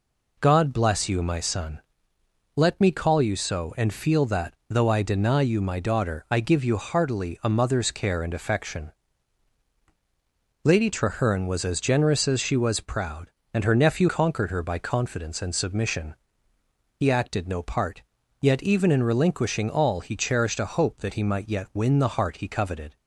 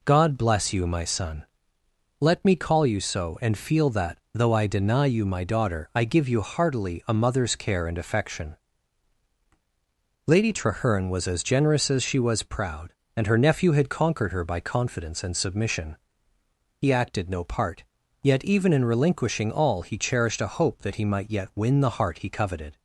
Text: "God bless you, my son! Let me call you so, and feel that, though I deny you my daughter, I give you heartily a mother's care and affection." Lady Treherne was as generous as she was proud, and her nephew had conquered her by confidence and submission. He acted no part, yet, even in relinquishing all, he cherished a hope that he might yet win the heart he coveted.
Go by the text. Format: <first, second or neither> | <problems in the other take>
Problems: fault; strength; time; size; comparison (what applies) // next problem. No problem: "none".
second | skips "had"; at 14.0 s